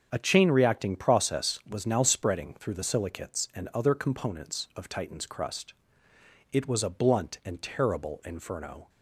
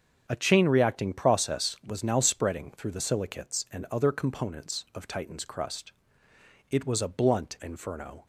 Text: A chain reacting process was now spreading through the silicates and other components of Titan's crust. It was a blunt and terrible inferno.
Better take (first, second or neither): first